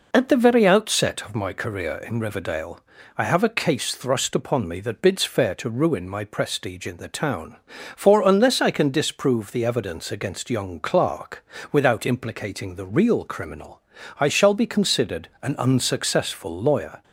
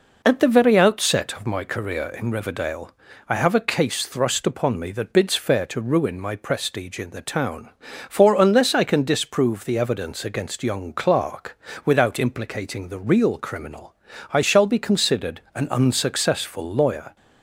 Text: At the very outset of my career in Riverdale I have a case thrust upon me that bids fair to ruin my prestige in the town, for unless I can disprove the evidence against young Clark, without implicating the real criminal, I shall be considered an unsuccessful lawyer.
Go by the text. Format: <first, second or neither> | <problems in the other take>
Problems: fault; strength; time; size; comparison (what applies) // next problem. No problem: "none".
neither | pauses between "Riverdale" and "I"; slight; the same in both